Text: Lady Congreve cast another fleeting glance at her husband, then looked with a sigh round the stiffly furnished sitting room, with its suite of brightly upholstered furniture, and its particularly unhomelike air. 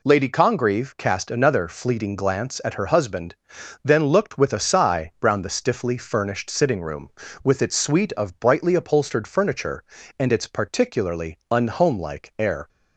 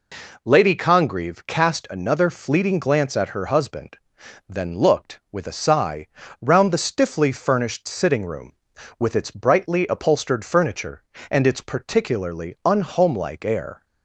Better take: first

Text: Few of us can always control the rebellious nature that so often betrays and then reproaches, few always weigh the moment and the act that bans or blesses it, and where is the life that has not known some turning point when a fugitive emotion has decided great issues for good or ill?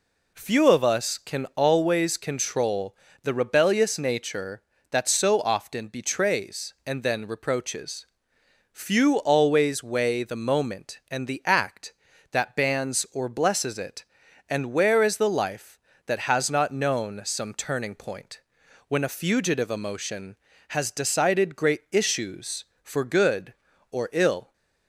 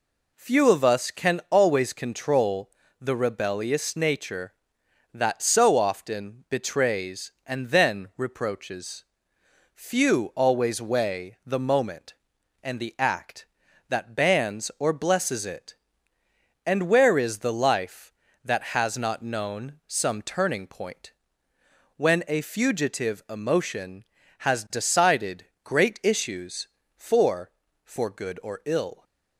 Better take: first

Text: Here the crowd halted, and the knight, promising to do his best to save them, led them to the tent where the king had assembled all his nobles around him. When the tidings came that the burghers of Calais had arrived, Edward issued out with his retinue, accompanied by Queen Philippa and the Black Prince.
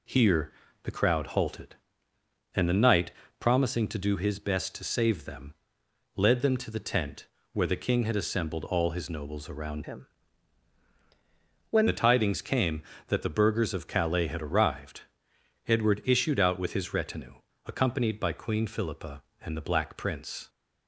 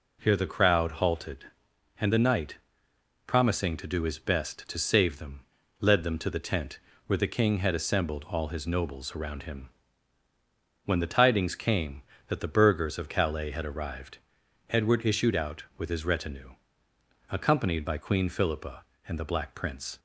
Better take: second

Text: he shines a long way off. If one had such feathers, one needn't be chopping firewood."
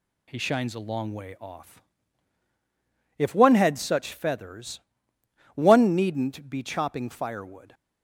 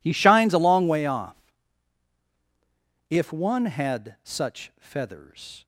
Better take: first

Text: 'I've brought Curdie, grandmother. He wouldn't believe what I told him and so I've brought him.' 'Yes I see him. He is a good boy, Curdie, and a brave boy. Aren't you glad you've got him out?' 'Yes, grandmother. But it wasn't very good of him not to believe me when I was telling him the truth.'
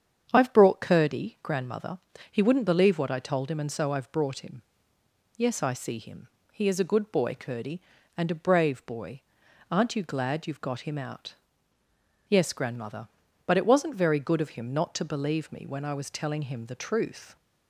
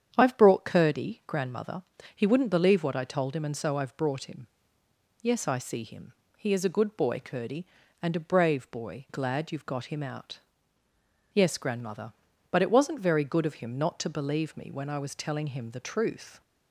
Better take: first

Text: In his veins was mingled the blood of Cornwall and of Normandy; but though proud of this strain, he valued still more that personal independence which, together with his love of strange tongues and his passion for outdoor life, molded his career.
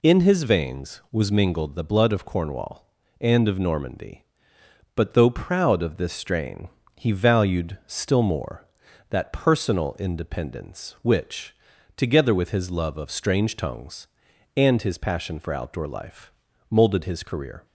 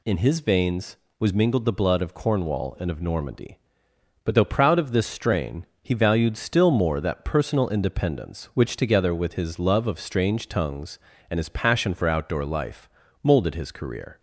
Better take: neither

